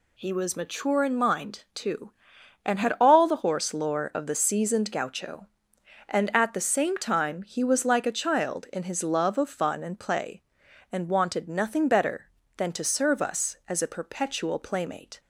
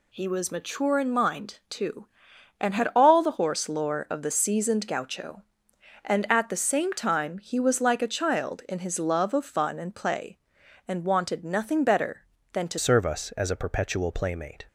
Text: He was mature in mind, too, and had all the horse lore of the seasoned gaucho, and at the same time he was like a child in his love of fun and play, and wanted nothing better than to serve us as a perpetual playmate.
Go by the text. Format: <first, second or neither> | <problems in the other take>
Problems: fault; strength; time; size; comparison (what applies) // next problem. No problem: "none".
first | changes voice at "serve"; from 12.7 s on; 1.9 s long